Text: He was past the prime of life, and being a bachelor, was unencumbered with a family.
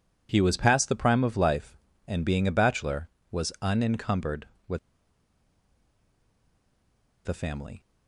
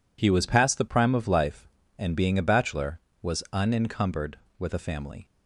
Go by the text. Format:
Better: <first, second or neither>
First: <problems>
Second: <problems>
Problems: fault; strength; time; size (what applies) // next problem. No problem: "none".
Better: second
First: pauses between "with" and "a"; strong; at 4.7 s; 2.4 s long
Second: none